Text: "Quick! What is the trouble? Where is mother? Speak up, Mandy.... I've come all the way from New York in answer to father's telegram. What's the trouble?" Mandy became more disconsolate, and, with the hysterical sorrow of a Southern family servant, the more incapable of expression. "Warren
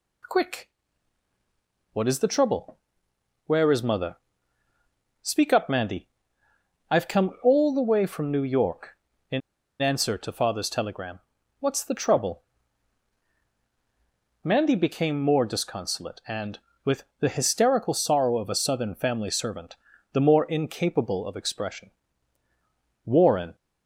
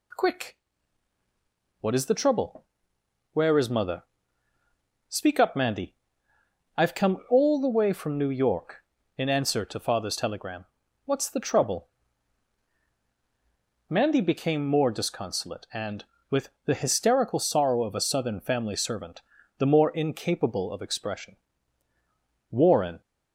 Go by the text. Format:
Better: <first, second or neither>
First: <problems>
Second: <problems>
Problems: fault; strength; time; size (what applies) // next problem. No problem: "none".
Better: second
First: pauses between "in" and "answer"; at 9.4 s; 0.40 s long // pauses between "with" and "the"; slight; at 17.0 s; 0.16 s long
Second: pauses between "with" and "the"; slight; at 16.5 s; 0.16 s long